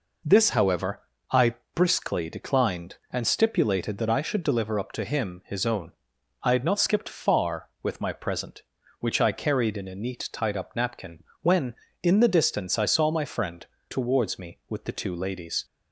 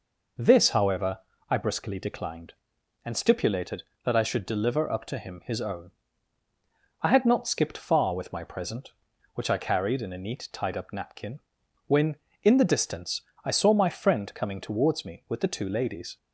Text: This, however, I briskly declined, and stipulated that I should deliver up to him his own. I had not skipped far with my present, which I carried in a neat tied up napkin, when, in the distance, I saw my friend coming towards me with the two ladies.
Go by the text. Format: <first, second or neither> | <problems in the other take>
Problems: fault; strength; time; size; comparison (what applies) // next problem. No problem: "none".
second | pauses between "I" and "briskly"; slight; at 1.5 s; 0.20 s long // skips "coming"; at 13.7 s